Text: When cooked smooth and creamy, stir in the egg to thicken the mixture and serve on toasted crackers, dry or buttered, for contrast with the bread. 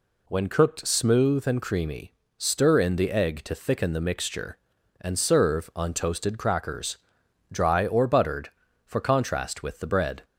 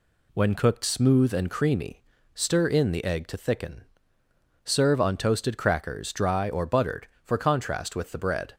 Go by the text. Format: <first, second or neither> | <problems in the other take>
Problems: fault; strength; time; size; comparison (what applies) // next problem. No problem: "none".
first | skips "the mixture and"; at 4.2 s